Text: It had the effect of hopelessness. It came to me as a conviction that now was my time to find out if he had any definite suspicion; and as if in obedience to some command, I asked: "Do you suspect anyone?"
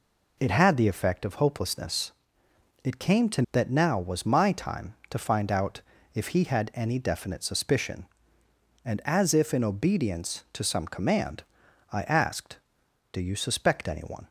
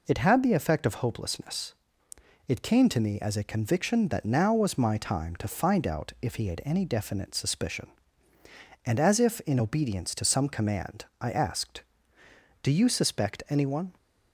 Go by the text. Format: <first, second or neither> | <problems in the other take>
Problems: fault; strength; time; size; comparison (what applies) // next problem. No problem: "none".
second | skips "me as a conviction"; at 3.4 s // pauses between "out" and "if"; slight; at 5.8 s; 0.34 s long